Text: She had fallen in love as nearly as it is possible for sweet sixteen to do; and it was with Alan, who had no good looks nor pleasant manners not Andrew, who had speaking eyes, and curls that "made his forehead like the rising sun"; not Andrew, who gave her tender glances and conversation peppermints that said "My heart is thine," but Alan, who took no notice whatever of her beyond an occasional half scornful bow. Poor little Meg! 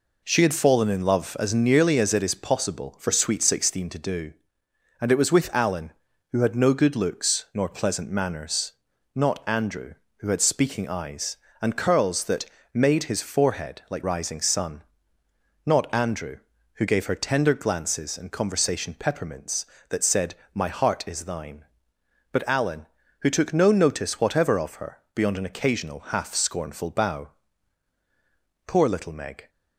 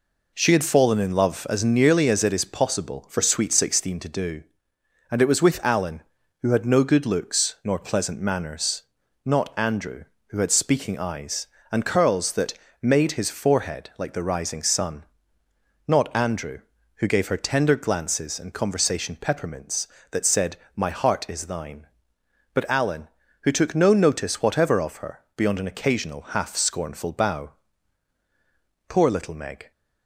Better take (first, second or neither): second